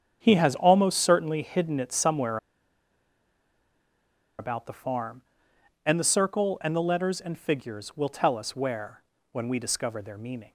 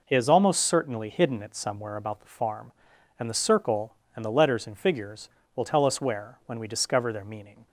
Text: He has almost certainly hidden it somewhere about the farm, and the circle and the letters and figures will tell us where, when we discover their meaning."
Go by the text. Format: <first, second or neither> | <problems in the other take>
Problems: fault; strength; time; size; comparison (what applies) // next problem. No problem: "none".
second | starts louder than the rest; strong; until 1.2 s; 8 dB // pauses between "somewhere" and "about"; strong; at 2.3 s; 2.0 s long